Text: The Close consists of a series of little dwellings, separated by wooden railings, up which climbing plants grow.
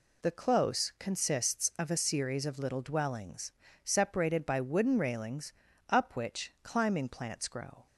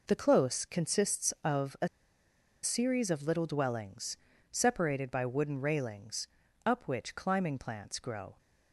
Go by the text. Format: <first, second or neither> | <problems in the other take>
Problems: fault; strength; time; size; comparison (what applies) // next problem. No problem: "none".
first | pauses between "a" and "series"; noticeable; at 1.8 s; 0.75 s long